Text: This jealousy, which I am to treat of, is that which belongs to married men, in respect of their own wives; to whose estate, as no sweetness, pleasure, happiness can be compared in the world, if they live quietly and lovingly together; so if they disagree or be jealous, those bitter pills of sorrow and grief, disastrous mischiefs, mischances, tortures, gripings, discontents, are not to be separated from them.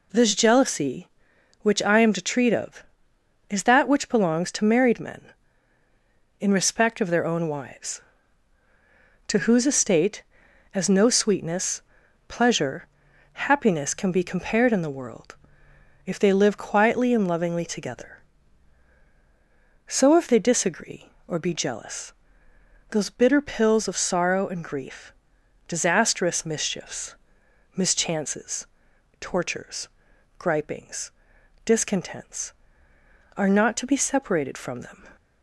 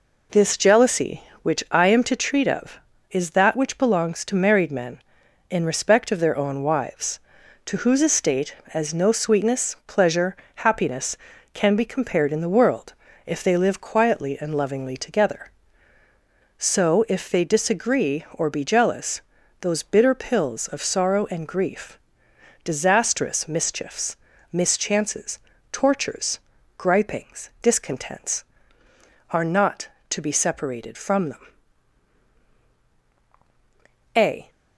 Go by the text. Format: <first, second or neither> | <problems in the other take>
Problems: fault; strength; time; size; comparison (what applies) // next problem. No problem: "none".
first | goes on to say "A"; slight; from 34.1 s on; 0.34 s long